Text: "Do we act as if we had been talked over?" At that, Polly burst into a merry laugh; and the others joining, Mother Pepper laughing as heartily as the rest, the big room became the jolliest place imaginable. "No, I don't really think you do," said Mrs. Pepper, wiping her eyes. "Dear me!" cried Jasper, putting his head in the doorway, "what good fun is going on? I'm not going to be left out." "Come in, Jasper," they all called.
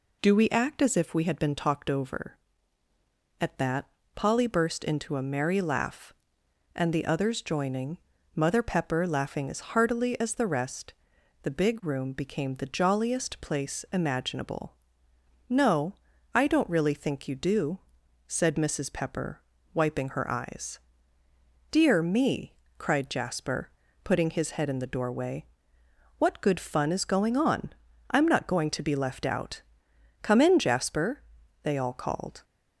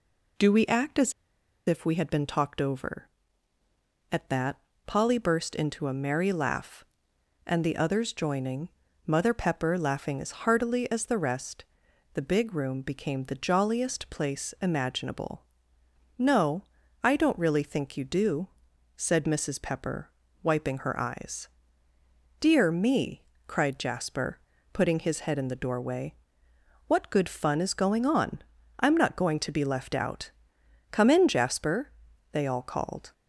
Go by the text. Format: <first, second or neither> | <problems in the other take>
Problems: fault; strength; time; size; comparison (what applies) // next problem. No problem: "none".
first | pauses between "as" and "if"; noticeable; at 1.1 s; 0.55 s long